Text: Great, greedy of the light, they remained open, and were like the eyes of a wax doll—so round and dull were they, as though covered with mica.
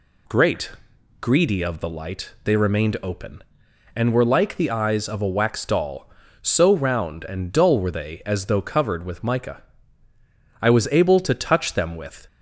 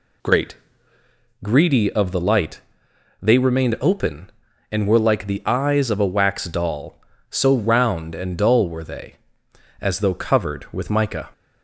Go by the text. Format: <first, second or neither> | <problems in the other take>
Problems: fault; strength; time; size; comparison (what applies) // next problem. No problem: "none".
second | goes on to say "I was able to touch them with"; from 10.6 s on; 1.6 s long